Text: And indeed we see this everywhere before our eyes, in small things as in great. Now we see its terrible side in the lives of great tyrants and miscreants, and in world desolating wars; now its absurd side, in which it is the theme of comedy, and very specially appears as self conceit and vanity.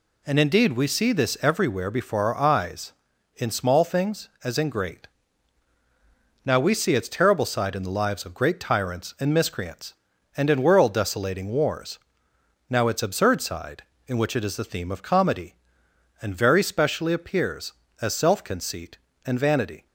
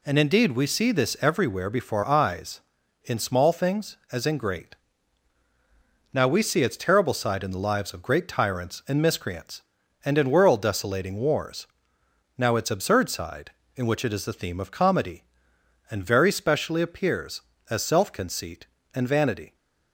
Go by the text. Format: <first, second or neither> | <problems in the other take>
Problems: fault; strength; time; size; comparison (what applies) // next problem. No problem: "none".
first | skips "our"; at 2.0 s